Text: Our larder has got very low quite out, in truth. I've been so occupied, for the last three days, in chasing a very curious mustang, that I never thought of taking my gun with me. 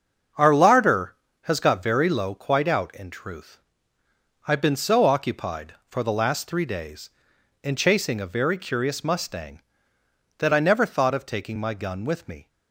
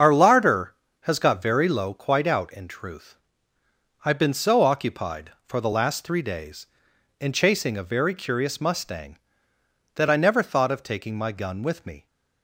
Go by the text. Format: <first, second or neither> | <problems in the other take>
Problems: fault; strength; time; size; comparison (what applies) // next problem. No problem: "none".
first | loses the start of "Our"; at 0.0 s; 60 ms // starts louder than the rest; until 1.2 s; 7 dB; also in the first